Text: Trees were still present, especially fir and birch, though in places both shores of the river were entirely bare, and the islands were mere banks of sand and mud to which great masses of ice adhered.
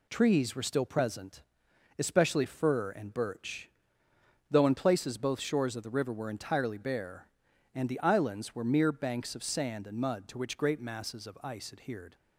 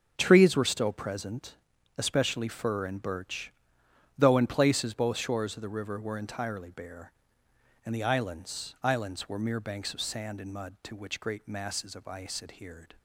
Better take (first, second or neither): first